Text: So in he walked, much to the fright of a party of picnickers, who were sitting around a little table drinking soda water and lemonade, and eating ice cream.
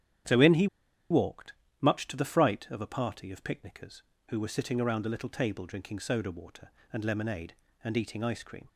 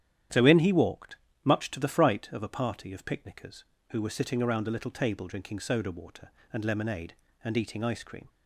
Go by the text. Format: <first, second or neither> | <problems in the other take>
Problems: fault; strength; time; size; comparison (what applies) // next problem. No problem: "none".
second | starts louder than the rest; strong; until 1.9 s; 10 dB; strong in the second // pauses between "he" and "walked"; at 0.6 s; 0.44 s long